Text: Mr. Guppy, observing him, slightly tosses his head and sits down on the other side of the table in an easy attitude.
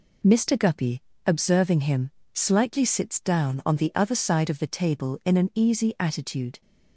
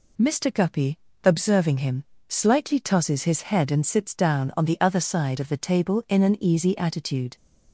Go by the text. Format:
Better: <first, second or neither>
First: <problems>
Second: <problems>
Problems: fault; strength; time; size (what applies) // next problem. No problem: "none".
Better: second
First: skips "tosses his head and"; at 2.8 s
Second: none